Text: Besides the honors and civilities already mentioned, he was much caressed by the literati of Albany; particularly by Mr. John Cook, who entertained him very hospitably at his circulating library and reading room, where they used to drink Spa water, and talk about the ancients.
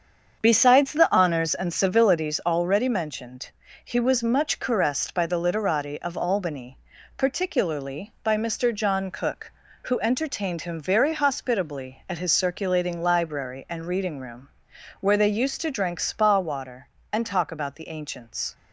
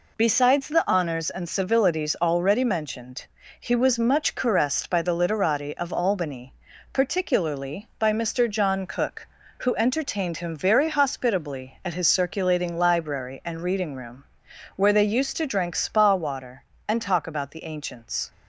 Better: second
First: starts louder than the rest; strong; until 2.3 s; 7 dB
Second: none

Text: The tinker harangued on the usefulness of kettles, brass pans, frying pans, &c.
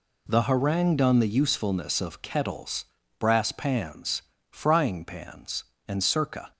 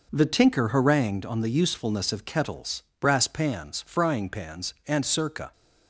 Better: second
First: skips "tinker"; at 0.4 s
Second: none

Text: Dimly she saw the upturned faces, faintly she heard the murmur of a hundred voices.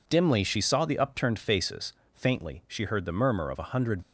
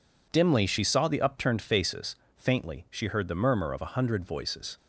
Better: second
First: stops before "voices"; at 4.0 s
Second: none

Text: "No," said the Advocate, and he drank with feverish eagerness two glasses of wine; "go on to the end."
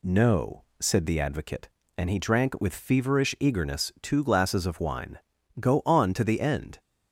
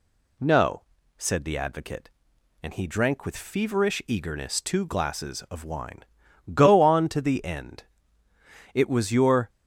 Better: first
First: none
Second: goes on to say "It was your"; noticeable; from 8.7 s on; 0.74 s long

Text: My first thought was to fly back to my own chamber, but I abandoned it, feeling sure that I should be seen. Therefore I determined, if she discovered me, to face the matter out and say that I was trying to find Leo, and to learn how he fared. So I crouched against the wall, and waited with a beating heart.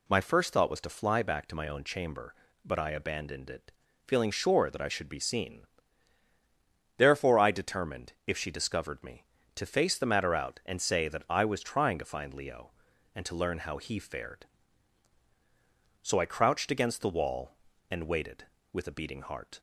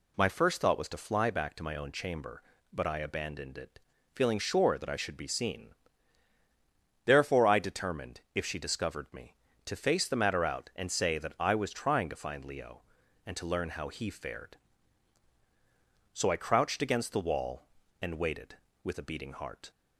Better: neither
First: none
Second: none

